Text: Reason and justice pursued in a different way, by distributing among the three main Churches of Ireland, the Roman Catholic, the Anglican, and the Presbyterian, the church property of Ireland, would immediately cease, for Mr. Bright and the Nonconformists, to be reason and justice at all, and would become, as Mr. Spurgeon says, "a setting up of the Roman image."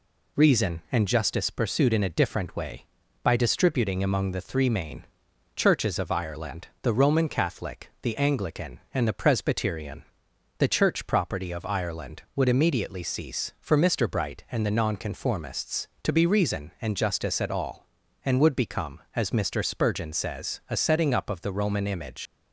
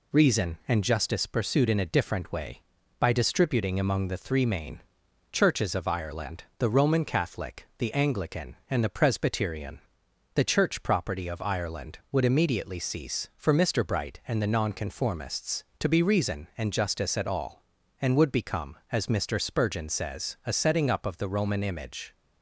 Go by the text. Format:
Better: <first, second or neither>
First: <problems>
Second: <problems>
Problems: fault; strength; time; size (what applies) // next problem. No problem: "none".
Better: second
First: pauses between "main" and "Churches"; noticeable; at 5.0 s; 0.50 s long // leaves "image" unfinished; at 22.2 s; 115 ms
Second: pauses between "main" and "Churches"; noticeable; at 4.8 s; 0.50 s long